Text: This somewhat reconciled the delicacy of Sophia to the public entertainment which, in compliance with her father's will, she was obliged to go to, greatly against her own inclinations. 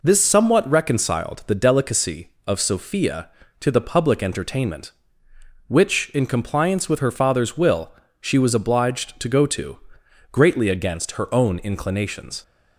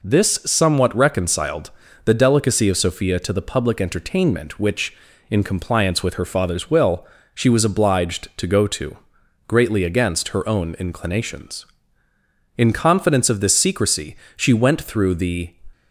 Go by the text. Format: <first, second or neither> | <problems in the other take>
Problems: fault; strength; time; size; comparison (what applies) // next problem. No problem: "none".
first | pauses between "reconciled" and "the"; slight; at 1.7 s; 0.34 s long // goes on to say "In confidence of this secrecy she went through the"; strong; from 12.5 s on; 2.9 s long